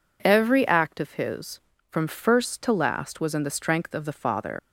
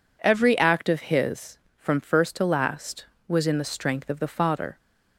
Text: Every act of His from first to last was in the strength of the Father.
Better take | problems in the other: second | leaves "Father" unfinished; at 4.5 s; 80 ms

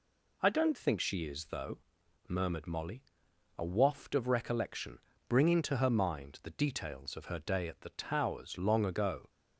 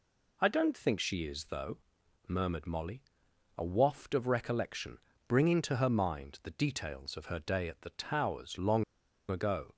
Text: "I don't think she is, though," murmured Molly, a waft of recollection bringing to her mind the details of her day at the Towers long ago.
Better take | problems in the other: first | pauses between "recollection" and "bringing"; slight; at 4.9 s; 0.30 s long; slight in the first // pauses between "long" and "ago"; at 8.8 s; 0.44 s long

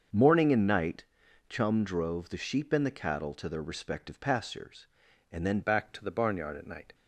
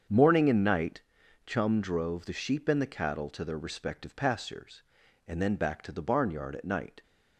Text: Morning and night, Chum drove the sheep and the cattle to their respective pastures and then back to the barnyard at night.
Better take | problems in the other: second | starts louder than the rest; until 1.5 s; 6.5 dB; strong in the second // changes voice at "back"; from 5.6 s on; 1.3 s long

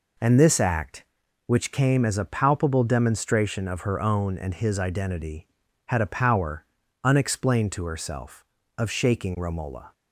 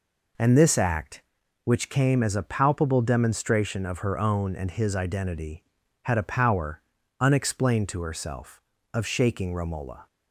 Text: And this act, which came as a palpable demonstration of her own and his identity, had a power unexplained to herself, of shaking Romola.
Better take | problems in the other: neither | pauses between "power" and "unexplained"; the same in both

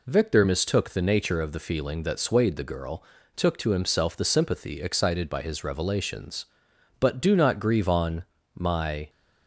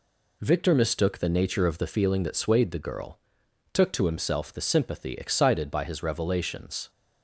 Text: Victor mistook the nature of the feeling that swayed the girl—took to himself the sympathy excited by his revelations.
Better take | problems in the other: second | goes on to say "But do not grieve on my"; strong; from 6.9 s on; 2.1 s long

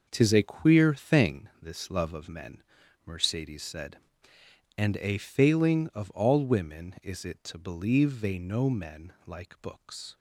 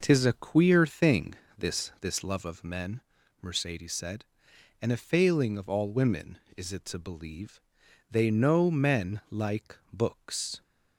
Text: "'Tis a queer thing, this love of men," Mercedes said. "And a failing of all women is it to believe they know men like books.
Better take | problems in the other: first | says "this" twice; at 1.9 s // pauses between "believe" and "they"; noticeable; at 7.6 s; 0.50 s long // pauses between "like" and "books"; slight; at 9.7 s; 0.16 s long

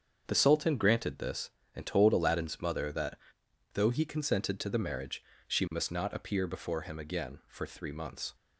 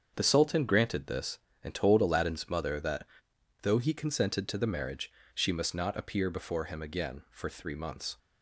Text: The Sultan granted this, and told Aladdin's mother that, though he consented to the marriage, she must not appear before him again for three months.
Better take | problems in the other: neither | starts louder than the rest; strong; the same in both

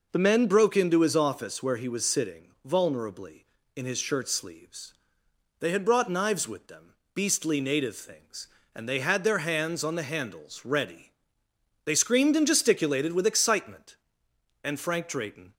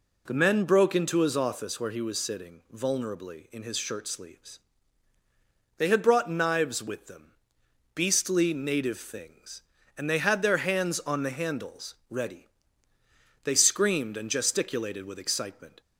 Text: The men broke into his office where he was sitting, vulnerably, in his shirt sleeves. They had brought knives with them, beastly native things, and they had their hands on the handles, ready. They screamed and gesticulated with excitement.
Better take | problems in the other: second | goes on to say "And Frank Drayton"; noticeable; from 14.6 s on; 0.90 s long

